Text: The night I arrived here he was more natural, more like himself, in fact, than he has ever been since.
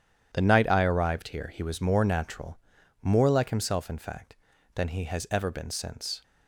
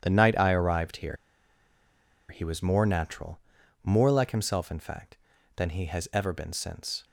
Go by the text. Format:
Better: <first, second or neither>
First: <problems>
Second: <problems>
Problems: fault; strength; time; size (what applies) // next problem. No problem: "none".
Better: first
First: starts louder than the rest; strong; until 1.3 s; 10 dB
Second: starts louder than the rest; strong; until 1.0 s; 10 dB // pauses between "here" and "he"; at 1.1 s; 1.1 s long